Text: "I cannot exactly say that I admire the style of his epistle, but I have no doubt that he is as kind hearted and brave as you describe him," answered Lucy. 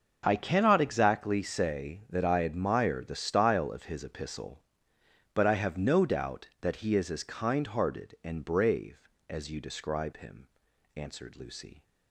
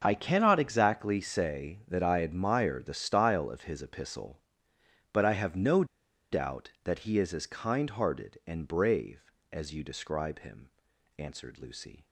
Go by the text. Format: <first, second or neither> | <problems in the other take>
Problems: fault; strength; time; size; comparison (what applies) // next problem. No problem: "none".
first | starts louder than the rest; until 1.0 s; 6 dB; also in the first // pauses between "no" and "doubt"; noticeable; at 5.8 s; 0.47 s long